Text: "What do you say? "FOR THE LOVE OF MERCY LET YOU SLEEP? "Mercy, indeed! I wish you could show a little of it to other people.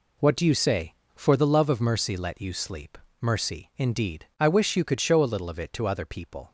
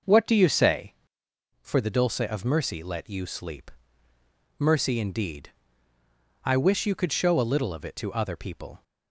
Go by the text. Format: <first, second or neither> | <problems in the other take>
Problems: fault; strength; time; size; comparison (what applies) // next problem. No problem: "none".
first | says "Dulce" for "LOVE"; at 1.8 s